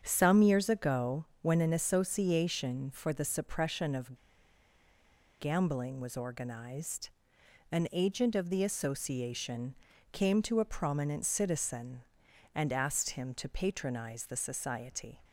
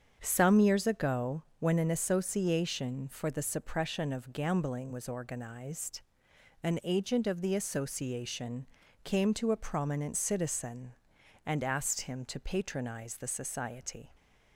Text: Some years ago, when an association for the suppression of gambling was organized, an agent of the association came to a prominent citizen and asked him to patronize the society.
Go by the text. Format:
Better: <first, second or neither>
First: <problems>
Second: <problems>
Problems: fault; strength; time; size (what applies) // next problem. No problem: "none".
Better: second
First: starts louder than the rest; strong; until 1.0 s; 7.5 dB // pauses between "of" and "gambling"; strong; at 4.1 s; 1.2 s long // pauses between "association" and "came"; at 9.7 s; 0.38 s long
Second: starts louder than the rest; strong; until 1.2 s; 7.5 dB // pauses between "association" and "came"; at 8.6 s; 0.38 s long